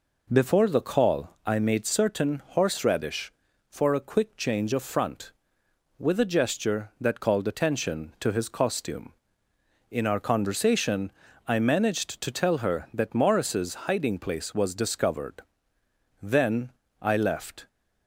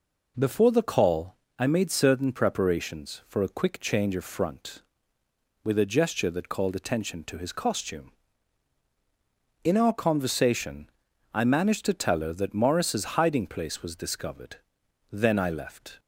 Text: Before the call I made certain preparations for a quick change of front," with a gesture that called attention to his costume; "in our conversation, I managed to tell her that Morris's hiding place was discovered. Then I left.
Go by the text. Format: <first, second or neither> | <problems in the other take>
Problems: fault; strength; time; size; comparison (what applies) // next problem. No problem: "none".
second | pauses between "call" and "I"; slight; at 1.3 s; 0.16 s long; slight in the second // says "horseradish" for "preparations"; at 2.4 s // pauses between "Then" and "I"; slight; at 16.7 s; 0.28 s long